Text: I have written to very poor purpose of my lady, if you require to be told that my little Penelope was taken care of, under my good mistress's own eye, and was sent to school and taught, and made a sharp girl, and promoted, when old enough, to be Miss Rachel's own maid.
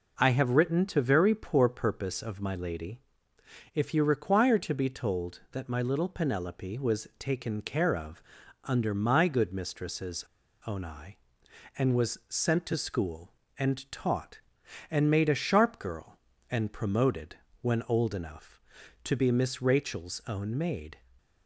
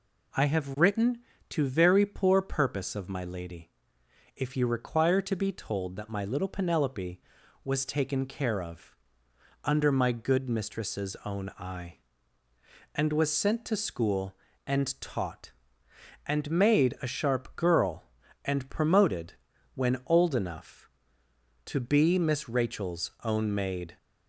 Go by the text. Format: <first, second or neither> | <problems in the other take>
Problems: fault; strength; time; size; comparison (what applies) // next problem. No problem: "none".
second | pauses between "mistress's" and "own"; at 10.2 s; 0.42 s long